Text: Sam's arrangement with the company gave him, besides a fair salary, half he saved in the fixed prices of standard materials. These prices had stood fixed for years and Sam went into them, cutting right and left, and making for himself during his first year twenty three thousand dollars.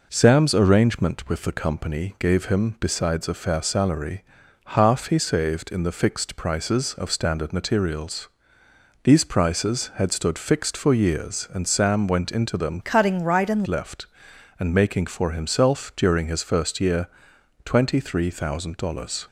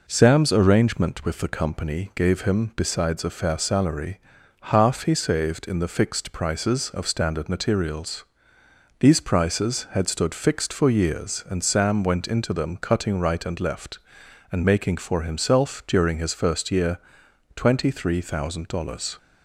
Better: second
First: changes voice from "cutting" to "and"; from 12.8 to 13.6 s; 0.8 s long // pauses between "year" and "twenty"; noticeable; at 17.0 s; 0.58 s long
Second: pauses between "year" and "twenty"; noticeable; at 16.9 s; 0.58 s long

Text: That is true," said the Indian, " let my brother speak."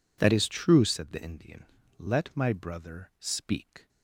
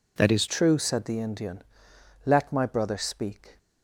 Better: first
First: none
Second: changes voice at "true"; from 0.4 s on; 3.1 s long

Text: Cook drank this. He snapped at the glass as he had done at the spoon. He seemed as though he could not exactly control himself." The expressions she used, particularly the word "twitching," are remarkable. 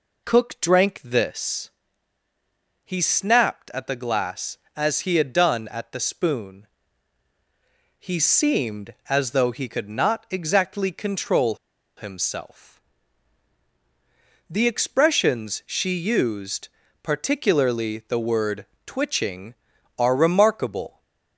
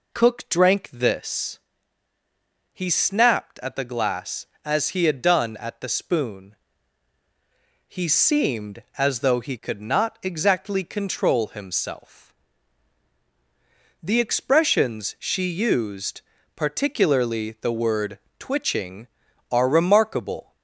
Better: second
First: pauses between "control" and "himself"; at 11.5 s; 0.42 s long // pauses between "word" and "twitching"; slight; at 18.6 s; 0.20 s long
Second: pauses between "word" and "twitching"; slight; at 18.1 s; 0.20 s long

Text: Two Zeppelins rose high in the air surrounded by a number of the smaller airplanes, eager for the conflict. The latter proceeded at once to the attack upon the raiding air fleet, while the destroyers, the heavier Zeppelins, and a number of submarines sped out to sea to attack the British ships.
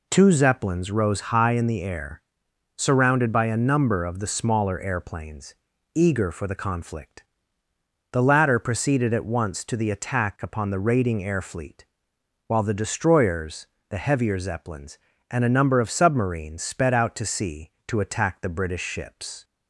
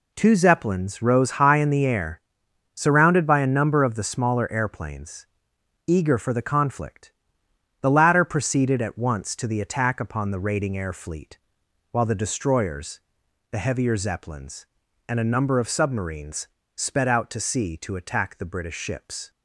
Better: first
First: pauses between "air" and "surrounded"; noticeable; at 2.2 s; 0.58 s long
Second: pauses between "air" and "surrounded"; noticeable; at 2.2 s; 0.54 s long // pauses between "submarines" and "sped"; slight; at 16.4 s; 0.27 s long

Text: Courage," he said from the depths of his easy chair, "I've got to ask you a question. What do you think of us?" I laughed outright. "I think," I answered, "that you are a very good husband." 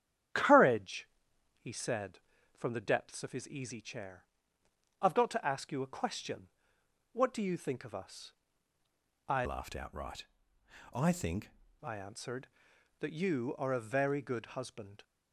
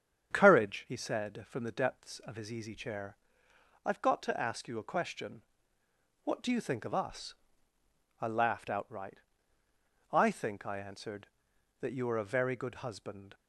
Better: second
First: starts louder than the rest; strong; until 1.8 s; 9.5 dB // changes voice from "laughed" to "think"; from 9.4 to 11.4 s; 2.0 s long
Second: starts louder than the rest; strong; until 1.3 s; 7.5 dB

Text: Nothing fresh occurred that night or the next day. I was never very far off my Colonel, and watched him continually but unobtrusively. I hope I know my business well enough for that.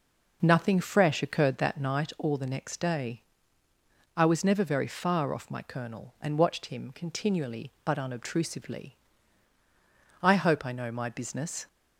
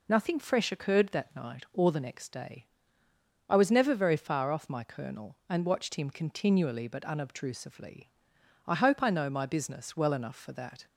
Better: second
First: stops before "well enough for that"; at 11.6 s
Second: none

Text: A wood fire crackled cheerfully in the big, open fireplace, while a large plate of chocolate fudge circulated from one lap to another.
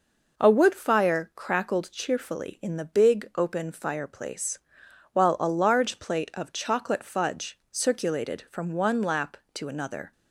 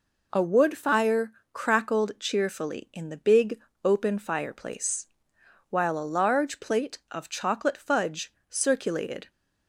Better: first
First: none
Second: pauses between "fire" and "crackled"; slight; at 1.3 s; 0.20 s long // pauses between "fudge" and "circulated"; slight; at 8.3 s; 0.16 s long // stops before "from one lap to another"; at 9.2 s

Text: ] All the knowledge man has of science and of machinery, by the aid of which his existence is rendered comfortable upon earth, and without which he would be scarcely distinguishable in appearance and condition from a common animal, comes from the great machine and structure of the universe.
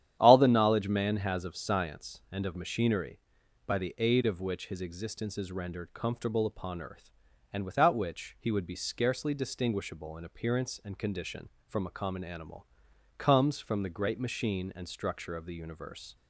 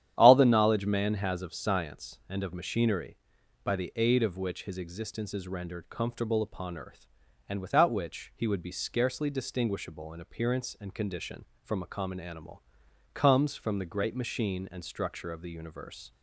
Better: neither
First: starts louder than the rest; strong; until 1.2 s; 10.5 dB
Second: starts louder than the rest; strong; until 1.1 s; 10.5 dB

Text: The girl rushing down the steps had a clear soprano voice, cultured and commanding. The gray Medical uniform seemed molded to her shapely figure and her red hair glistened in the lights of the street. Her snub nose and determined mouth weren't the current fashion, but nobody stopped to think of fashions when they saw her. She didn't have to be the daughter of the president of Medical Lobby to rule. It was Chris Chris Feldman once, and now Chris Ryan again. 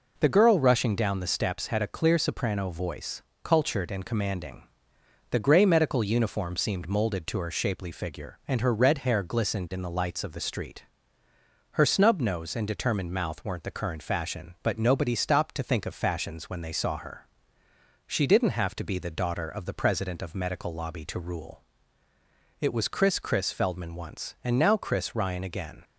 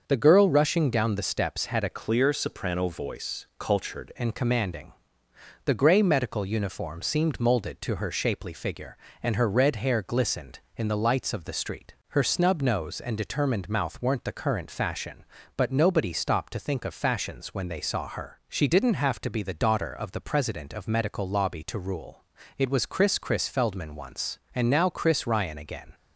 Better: first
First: none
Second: starts louder than the rest; until 1.0 s; 6.5 dB // changes voice from "clear" to "cultured"; from 1.9 to 4.1 s; 2.2 s long

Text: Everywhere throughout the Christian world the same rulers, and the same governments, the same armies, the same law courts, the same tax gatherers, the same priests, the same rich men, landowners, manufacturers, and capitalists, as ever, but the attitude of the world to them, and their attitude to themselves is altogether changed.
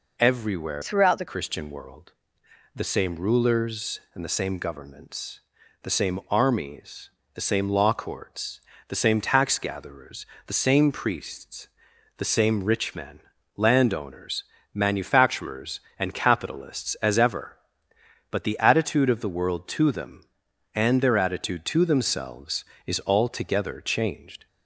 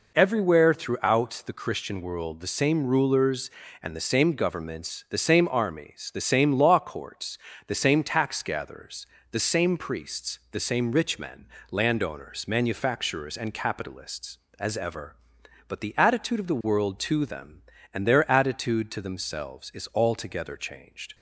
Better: second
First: changes voice from "throughout" to "the"; from 0.8 to 1.2 s; 0.4 s long // pauses between "world" and "the"; noticeable; at 2.1 s; 0.64 s long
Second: none

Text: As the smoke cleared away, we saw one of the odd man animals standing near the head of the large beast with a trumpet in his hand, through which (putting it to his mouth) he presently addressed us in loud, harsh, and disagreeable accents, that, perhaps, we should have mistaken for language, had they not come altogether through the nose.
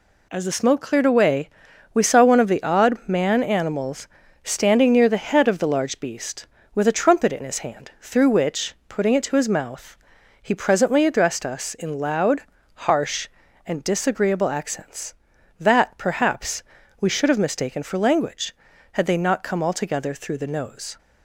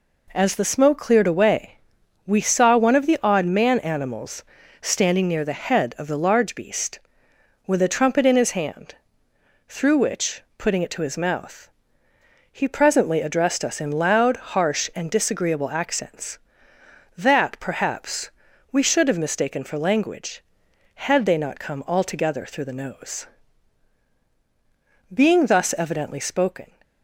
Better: first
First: pauses between "animals" and "standing"; slight; at 4.0 s; 0.36 s long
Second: pauses between "animals" and "standing"; at 4.4 s; 0.38 s long // goes on to say "Being thus evidently spoken"; from 25.1 s on; 1.5 s long

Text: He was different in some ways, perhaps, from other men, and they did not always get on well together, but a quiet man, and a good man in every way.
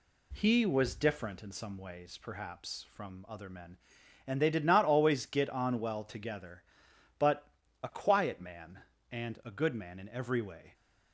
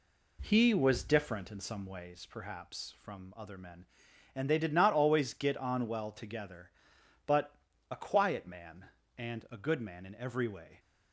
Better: first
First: pauses between "but" and "a"; slight; at 7.4 s; 0.36 s long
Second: starts louder than the rest; slight; until 2.2 s; 2.5 dB // pauses between "but" and "a"; slight; at 7.5 s; 0.36 s long

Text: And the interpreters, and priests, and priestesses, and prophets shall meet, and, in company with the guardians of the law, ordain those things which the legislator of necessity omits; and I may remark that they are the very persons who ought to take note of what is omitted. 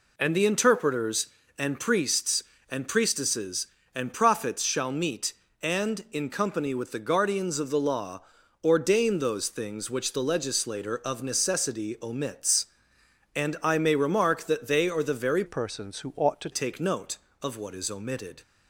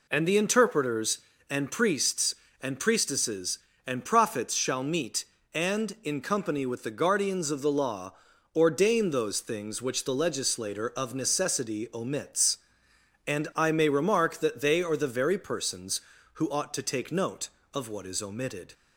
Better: second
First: changes voice from "persons" to "to"; from 15.4 to 16.4 s; 1.0 s long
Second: none

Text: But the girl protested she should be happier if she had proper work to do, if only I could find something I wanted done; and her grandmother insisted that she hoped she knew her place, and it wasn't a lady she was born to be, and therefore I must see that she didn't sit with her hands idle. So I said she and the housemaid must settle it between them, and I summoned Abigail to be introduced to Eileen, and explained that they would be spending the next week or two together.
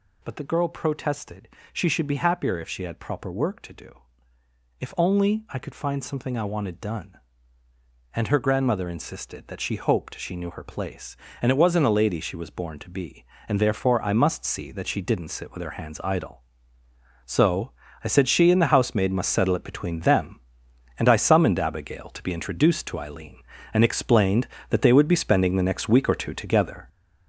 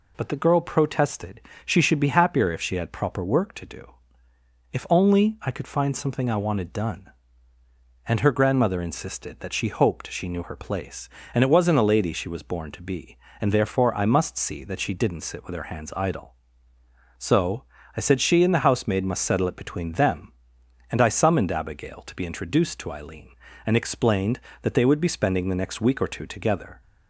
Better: second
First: gets louder; throughout; 7 dB // pauses between "protested" and "she"; slight; at 1.4 s; 0.24 s long // pauses between "So" and "I"; slight; at 17.7 s; 0.32 s long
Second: pauses between "protested" and "she"; slight; at 1.4 s; 0.24 s long // pauses between "So" and "I"; slight; at 17.6 s; 0.32 s long

